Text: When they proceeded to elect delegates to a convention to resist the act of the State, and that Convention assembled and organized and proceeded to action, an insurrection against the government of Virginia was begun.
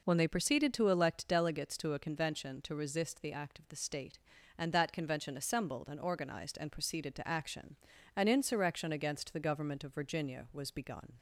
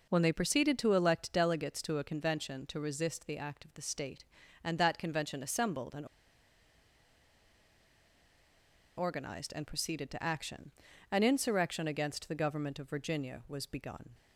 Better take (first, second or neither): first